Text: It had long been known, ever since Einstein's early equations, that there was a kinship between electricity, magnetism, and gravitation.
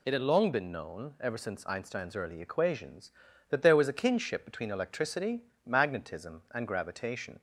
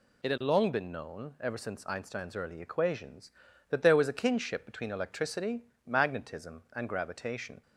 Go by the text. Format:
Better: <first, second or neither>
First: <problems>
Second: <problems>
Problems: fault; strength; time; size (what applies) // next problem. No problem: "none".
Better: neither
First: none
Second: none